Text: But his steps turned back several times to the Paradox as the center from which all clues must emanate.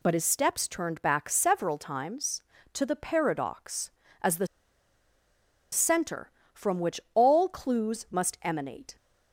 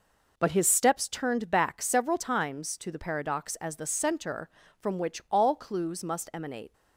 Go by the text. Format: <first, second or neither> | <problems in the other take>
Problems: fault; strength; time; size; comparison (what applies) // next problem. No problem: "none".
second | pauses between "the" and "center"; strong; at 4.4 s; 1.2 s long